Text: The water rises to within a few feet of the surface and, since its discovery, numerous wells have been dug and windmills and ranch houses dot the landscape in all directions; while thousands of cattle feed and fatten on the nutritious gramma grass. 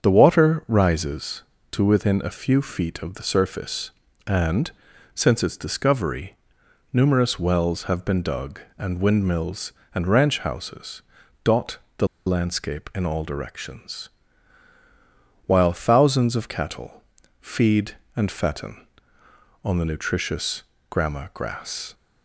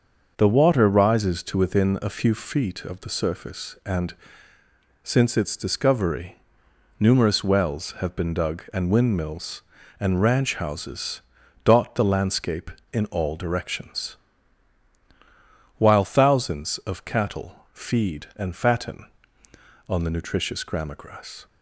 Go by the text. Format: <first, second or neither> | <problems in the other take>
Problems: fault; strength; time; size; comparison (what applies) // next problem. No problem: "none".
second | starts louder than the rest; strong; until 1.1 s; 7 dB; also in the second // pauses between "houses" and "dot"; at 11.0 s; 0.40 s long; also in the second // pauses between "dot" and "the"; slight; at 11.7 s; 0.18 s long // pauses between "the" and "landscape"; slight; at 12.0 s; 0.19 s long // pauses between "cattle" and "feed"; slight; at 17.0 s; 0.36 s long // pauses between "nutritious" and "gramma"; slight; at 20.6 s; 0.26 s long